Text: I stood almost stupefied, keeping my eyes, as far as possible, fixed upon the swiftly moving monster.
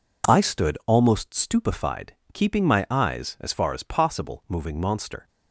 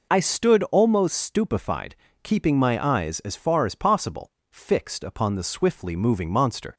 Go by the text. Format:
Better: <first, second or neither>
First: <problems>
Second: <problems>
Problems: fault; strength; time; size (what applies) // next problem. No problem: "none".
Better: second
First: skips "fixed upon the swiftly"; at 4.4 s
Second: none